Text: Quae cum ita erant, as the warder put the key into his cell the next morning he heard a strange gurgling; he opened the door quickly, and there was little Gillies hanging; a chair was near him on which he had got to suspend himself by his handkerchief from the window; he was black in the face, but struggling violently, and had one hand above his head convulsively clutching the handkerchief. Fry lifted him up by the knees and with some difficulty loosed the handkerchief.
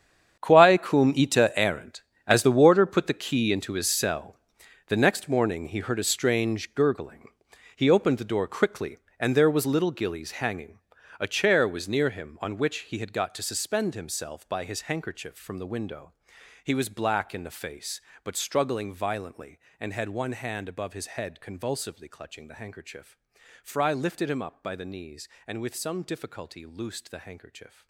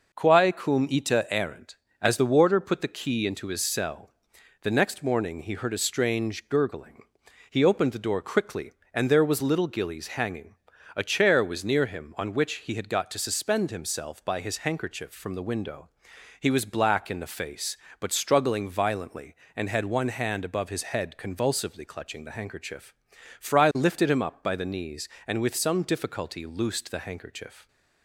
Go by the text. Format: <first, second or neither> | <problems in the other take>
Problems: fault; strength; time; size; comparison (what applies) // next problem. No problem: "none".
second | gets quieter; strong; throughout; 15.5 dB // pauses between "cell" and "the"; noticeable; at 4.3 s; 0.50 s long; noticeable in the second